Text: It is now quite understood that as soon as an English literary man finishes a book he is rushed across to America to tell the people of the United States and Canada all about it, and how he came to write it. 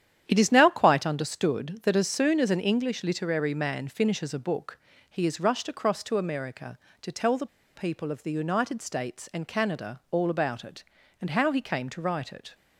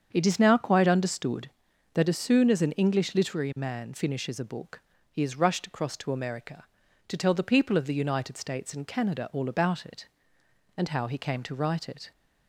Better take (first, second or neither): second